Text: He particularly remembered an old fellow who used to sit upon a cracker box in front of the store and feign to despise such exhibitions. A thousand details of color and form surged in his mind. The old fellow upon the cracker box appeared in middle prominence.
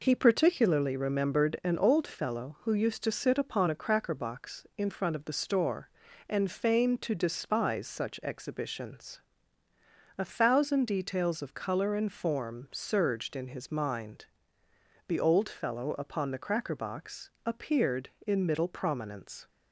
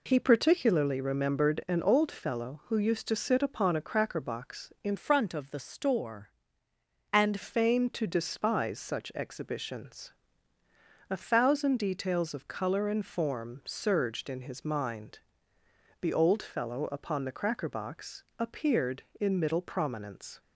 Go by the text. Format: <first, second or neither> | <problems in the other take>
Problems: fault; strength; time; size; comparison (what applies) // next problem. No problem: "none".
first | changes voice from "front" to "and"; from 4.9 to 7.4 s; 2.5 s long // pauses between "box" and "appeared"; slight; at 18.2 s; 0.16 s long; slight in the first